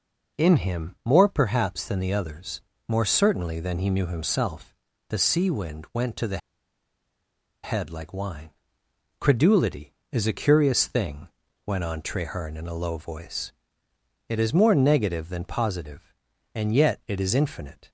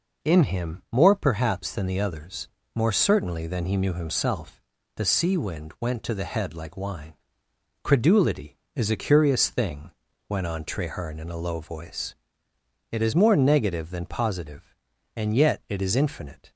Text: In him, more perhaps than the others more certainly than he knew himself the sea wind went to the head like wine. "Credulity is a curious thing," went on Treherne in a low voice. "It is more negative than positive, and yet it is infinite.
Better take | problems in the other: second | pauses between "others" and "more"; slight; at 2.6 s; 0.26 s long; slight in the second // pauses between "himself" and "the"; slight; at 4.7 s; 0.34 s long; slight in the second // pauses between "the" and "head"; strong; at 6.3 s; 1.2 s long

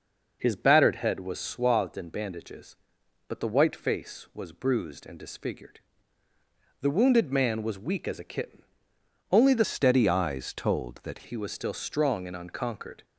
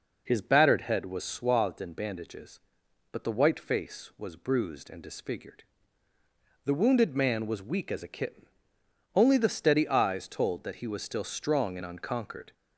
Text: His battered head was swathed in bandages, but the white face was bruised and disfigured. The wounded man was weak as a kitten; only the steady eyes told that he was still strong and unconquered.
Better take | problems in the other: second | changes voice from "steady" to "that"; from 9.6 to 11.2 s; 1.6 s long

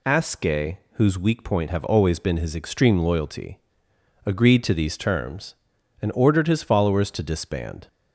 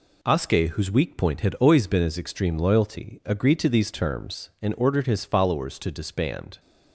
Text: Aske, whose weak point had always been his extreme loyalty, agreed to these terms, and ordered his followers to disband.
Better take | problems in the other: second | says "have" for "had"; at 1.6 s

